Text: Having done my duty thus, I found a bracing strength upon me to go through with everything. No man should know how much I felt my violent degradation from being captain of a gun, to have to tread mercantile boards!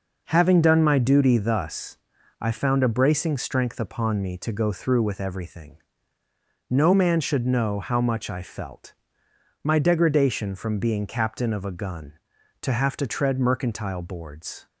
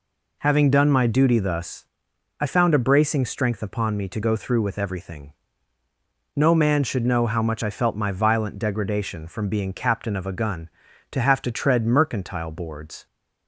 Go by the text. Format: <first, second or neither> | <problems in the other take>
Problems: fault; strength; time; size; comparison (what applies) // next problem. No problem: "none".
second | pauses between "felt" and "my"; noticeable; at 8.9 s; 0.72 s long // skips "violent"; at 9.7 s